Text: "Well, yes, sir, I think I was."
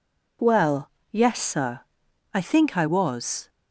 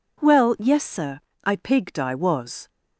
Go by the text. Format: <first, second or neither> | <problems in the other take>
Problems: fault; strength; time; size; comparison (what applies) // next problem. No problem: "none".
first | says "pigged" for "think"; at 1.5 s